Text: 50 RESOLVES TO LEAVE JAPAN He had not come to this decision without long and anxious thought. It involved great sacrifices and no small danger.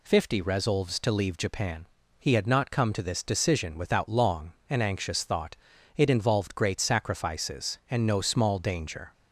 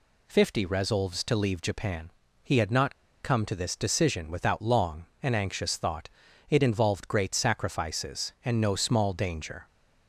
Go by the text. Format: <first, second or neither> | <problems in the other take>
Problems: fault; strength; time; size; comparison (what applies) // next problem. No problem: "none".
first | pauses between "JAPAN" and "He"; slight; at 2.1 s; 0.32 s long; slight in the first // pauses between "not" and "come"; slight; at 2.9 s; 0.27 s long